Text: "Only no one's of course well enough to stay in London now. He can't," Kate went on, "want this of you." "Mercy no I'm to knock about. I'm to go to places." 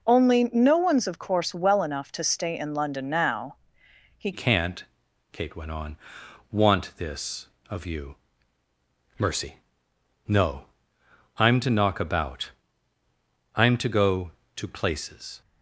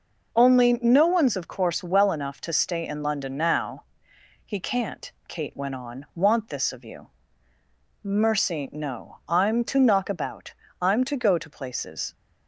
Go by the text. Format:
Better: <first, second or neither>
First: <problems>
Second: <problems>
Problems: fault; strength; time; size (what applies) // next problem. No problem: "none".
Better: second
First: changes voice at "can't"; from 4.3 s on; 11.1 s long // pauses between "Mercy" and "no"; noticeable; at 9.5 s; 0.70 s long // pauses between "no" and "I'm"; noticeable; at 10.6 s; 0.72 s long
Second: none